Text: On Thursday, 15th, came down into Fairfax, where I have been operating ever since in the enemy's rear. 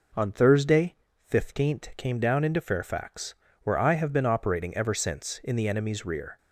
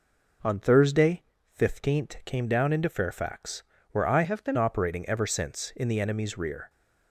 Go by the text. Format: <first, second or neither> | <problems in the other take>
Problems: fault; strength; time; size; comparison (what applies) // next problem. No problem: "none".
first | changes voice from "have" to "been"; from 4.2 to 4.5 s; 0.3 s long